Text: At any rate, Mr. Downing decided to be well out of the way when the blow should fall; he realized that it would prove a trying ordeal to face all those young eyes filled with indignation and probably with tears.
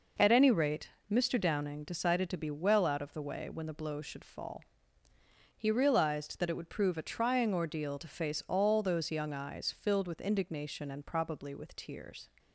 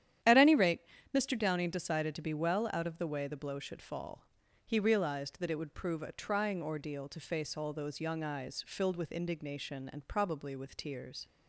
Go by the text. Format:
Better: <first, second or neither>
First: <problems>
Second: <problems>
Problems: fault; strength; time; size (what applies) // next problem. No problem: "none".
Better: first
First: none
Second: starts louder than the rest; strong; until 1.5 s; 10.5 dB // skips "when"; at 3.2 s